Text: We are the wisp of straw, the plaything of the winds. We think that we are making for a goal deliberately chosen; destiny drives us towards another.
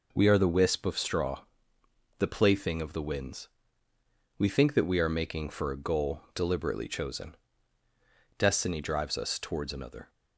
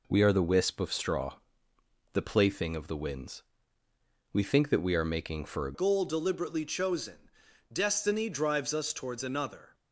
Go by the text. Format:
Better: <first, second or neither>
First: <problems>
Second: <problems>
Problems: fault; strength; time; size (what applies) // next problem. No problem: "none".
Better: first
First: none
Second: changes voice at "goal"; from 5.7 s on; 4.0 s long